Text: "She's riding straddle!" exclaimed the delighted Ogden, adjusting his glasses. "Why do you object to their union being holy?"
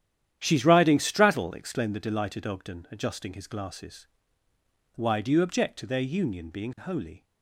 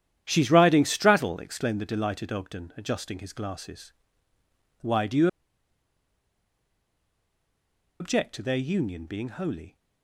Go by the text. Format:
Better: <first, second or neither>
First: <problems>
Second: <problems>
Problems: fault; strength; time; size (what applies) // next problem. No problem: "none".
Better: first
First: starts louder than the rest; strong; until 1.4 s; 10.5 dB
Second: starts louder than the rest; strong; until 1.2 s; 10.5 dB // pauses between "you" and "object"; strong; at 5.2 s; 2.7 s long